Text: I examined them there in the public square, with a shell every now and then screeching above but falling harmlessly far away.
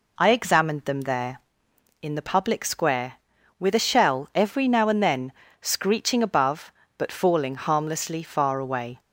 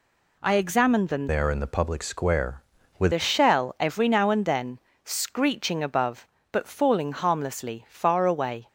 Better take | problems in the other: first | changes voice from "there" to "with"; from 1.2 to 3.1 s; 1.9 s long // pauses between "then" and "screeching"; slight; at 4.7 s; 0.26 s long; slight in the first

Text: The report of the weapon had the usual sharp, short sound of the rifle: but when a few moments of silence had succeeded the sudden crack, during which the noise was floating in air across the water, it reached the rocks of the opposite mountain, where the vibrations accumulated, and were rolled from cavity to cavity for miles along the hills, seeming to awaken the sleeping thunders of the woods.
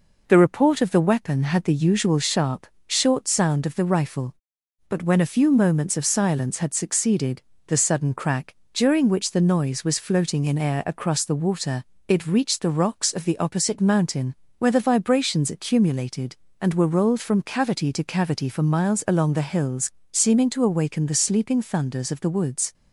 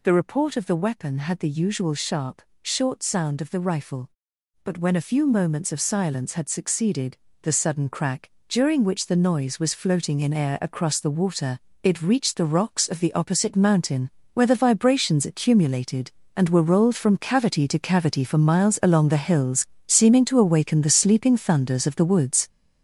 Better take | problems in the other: first | gets louder; throughout; 7 dB // pauses between "succeeded" and "the"; slight; at 7.1 s; 0.24 s long; slight in the first

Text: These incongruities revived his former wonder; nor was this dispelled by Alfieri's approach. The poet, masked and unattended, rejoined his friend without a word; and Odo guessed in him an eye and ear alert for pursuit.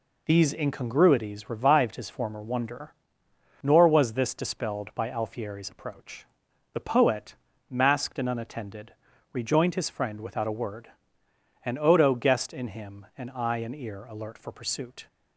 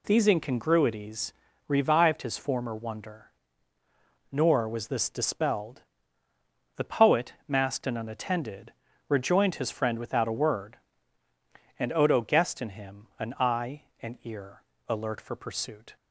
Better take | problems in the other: first | pauses between "incongruities" and "revived"; slight; at 1.3 s; 0.34 s long // skips "by Alfieri's approach"; at 6.2 s // pauses between "ear" and "alert"; slight; at 14.6 s; 0.26 s long

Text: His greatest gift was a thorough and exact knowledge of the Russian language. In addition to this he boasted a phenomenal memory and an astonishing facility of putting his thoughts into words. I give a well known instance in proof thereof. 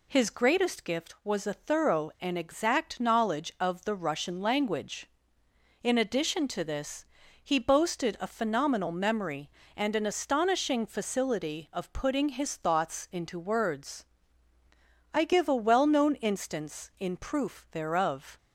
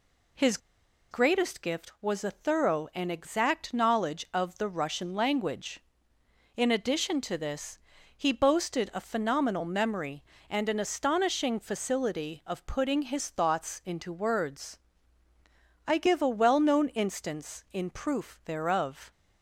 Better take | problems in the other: first | pauses between "His" and "greatest"; noticeable; at 0.5 s; 0.52 s long // pauses between "this" and "he"; at 7.7 s; 0.38 s long; also in the first

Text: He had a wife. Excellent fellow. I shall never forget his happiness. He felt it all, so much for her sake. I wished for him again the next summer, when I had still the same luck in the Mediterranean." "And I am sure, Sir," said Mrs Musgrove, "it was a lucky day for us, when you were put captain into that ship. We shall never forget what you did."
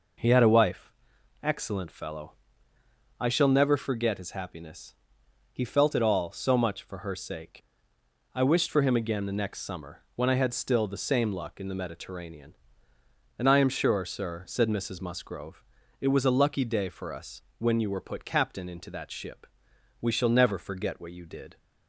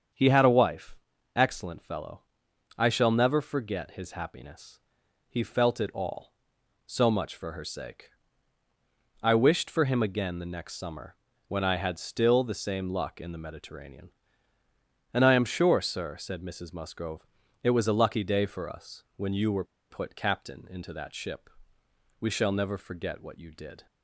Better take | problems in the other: first | starts louder than the rest; strong; until 1.5 s; 7.5 dB // pauses between "were" and "put"; slight; at 19.6 s; 0.25 s long

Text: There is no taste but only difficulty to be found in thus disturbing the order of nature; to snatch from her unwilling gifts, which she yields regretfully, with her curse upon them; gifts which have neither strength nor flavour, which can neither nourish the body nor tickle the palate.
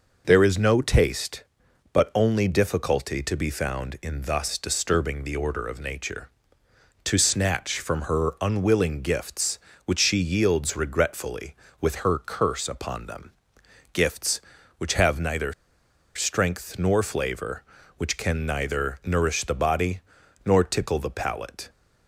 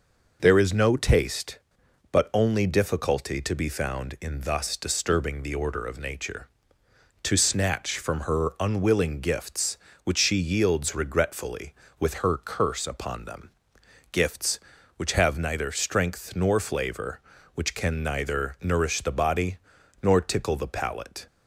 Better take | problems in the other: second | pauses between "neither" and "strength"; noticeable; at 15.5 s; 0.63 s long // pauses between "body" and "nor"; noticeable; at 19.9 s; 0.46 s long; noticeable in the second

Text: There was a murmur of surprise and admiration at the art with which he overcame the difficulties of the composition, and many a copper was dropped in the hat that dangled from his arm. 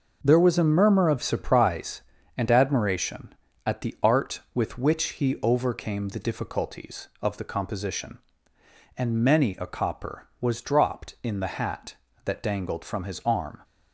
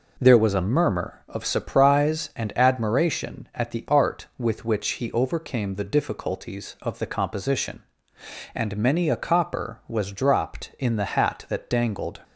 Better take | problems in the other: first | stops before "from his arm"; at 12.2 s

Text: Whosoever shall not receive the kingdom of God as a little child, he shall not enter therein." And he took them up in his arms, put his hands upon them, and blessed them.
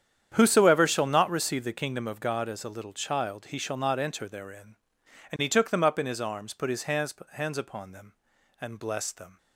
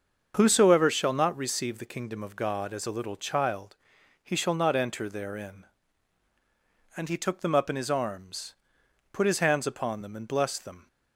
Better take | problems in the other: second | starts louder than the rest; strong; until 1.3 s; 9 dB; also in the second // says "hands" twice; at 7.3 s

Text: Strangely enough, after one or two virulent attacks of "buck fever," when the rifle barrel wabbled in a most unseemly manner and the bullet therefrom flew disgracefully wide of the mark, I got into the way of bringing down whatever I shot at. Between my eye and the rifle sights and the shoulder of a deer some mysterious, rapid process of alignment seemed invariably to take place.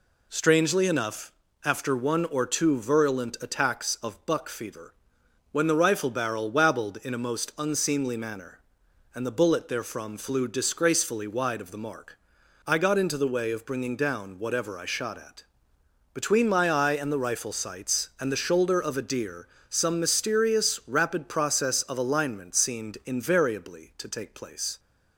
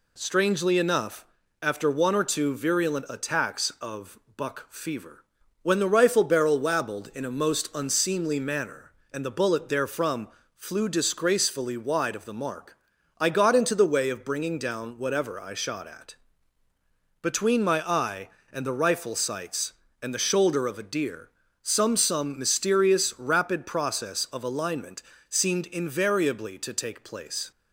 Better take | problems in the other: first | pauses between "of" and "buck"; slight; at 4.1 s; 0.16 s long // pauses between "therefrom" and "flew"; slight; at 10.2 s; 0.26 s long // pauses between "deer" and "some"; slight; at 21.2 s; 0.32 s long; slight in the first // says "some" twice; at 21.9 s // pauses between "alignment" and "seemed"; slight; at 25.0 s; 0.26 s long

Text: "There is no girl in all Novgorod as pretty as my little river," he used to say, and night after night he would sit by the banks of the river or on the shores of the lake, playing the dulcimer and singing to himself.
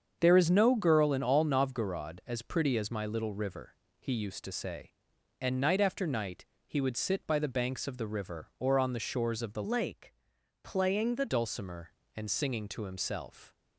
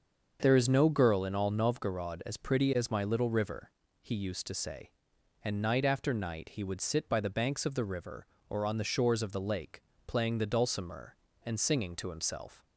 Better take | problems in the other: second | starts louder than the rest; strong; until 1.2 s; 7 dB; also in the second // pauses between "night" and "he"; slight; at 6.4 s; 0.22 s long // changes voice from "lake" to "the"; from 9.6 to 11.2 s; 1.6 s long

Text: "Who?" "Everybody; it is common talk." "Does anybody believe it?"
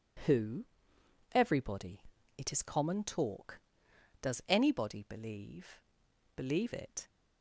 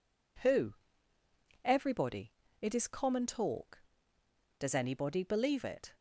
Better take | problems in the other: second | says "believe" twice; at 6.3 s

